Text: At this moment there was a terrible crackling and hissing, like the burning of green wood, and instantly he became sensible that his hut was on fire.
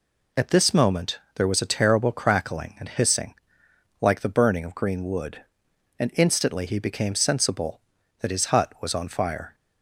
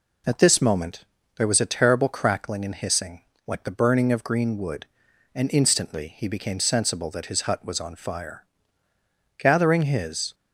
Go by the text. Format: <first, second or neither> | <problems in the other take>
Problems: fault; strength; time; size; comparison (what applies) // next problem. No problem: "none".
first | pauses between "moment" and "there"; slight; at 1.0 s; 0.32 s long; slight in the first // goes on to say "Gathering his"; noticeable; from 9.3 s on; 0.96 s long